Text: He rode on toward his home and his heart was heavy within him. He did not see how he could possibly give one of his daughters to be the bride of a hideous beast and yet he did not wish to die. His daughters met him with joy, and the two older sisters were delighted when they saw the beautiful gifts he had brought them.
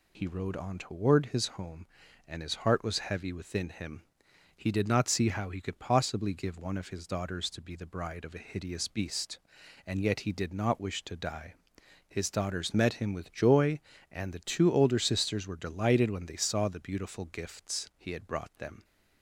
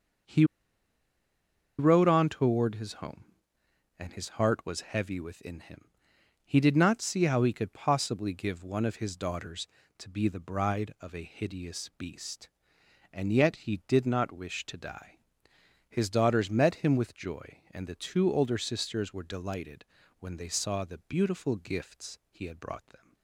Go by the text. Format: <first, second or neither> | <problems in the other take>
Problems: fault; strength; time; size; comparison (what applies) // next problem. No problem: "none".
first | starts louder than the rest; until 2.6 s; 6.5 dB // pauses between "He" and "rode"; strong; at 0.4 s; 1.3 s long // pauses between "delighted" and "when"; slight; at 19.8 s; 0.34 s long